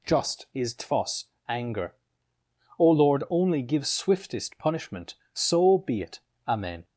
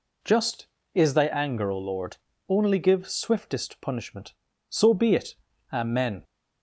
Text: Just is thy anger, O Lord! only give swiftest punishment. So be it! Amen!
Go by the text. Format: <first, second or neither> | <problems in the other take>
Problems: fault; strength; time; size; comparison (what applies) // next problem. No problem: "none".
second | says "tfos" for "thy"; at 0.7 s